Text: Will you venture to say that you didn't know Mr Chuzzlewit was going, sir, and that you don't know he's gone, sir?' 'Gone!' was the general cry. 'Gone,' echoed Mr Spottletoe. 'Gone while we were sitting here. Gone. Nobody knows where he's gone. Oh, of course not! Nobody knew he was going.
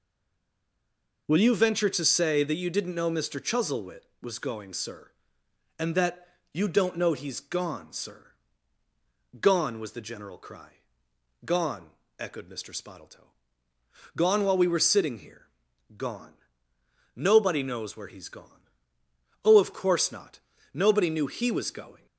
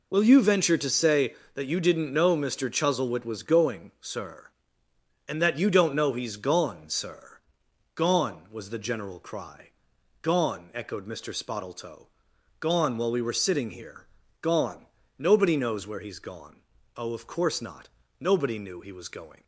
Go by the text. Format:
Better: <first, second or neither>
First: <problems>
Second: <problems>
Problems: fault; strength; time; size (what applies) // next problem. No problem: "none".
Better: second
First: stays silent before the first word; noticeable; until 1.2 s; 1.2 s long // pauses between "that" and "you"; slight; at 6.2 s; 0.26 s long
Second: none